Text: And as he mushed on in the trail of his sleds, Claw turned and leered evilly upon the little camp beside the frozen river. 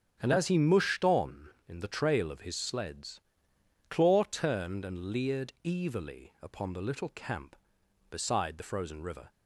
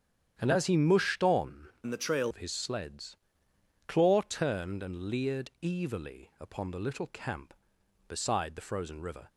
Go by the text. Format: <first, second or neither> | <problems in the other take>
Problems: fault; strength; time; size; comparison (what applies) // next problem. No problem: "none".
first | starts louder than the rest; strong; until 1.3 s; 9 dB; strong in the first // changes voice from "in" to "trail"; from 1.8 to 2.3 s; 0.5 s long